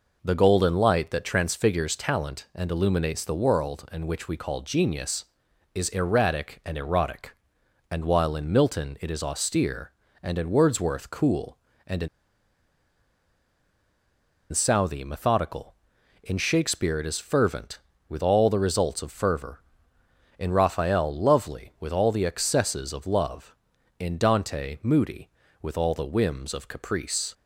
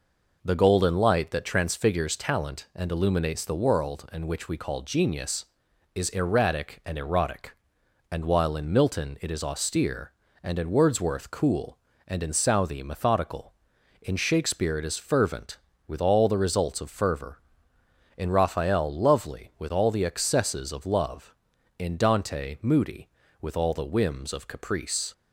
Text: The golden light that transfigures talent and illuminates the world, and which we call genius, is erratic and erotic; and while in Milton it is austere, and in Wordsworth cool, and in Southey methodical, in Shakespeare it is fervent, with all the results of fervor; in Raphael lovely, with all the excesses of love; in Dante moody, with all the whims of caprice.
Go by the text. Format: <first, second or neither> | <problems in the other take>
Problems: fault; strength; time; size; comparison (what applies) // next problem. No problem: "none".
second | pauses between "in" and "Southey"; strong; at 12.0 s; 2.4 s long